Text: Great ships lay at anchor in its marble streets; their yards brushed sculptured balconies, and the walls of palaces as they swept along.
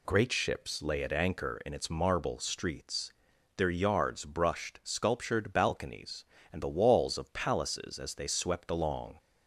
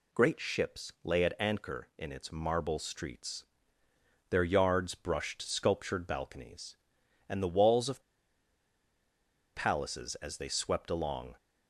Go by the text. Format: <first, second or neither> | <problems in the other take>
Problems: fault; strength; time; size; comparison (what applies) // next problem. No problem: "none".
first | pauses between "of" and "palaces"; strong; at 8.0 s; 1.5 s long